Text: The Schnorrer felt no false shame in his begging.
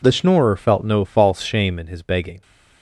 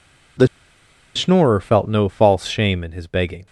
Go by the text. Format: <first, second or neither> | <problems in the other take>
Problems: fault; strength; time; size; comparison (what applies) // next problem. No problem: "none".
first | pauses between "The" and "Schnorrer"; noticeable; at 0.4 s; 0.69 s long